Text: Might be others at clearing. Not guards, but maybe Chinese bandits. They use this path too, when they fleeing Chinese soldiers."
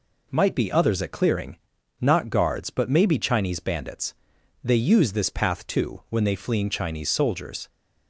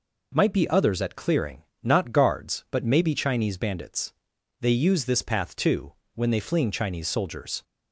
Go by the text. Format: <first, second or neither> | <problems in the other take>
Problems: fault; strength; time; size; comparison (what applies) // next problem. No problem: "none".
neither | none